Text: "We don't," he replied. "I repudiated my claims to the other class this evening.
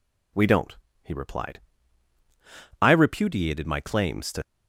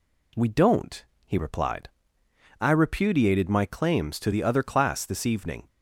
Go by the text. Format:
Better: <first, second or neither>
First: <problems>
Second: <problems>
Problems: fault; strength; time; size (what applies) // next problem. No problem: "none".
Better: second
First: stops before "the other class this evening"; at 4.4 s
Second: none